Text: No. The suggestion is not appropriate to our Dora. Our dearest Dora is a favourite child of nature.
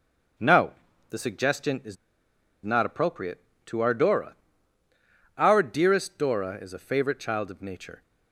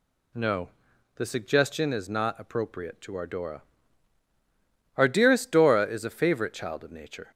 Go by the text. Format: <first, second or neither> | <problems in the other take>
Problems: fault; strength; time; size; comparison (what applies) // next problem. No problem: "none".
second | starts louder than the rest; until 1.7 s; 6.5 dB // pauses between "is" and "not"; noticeable; at 1.9 s; 0.67 s long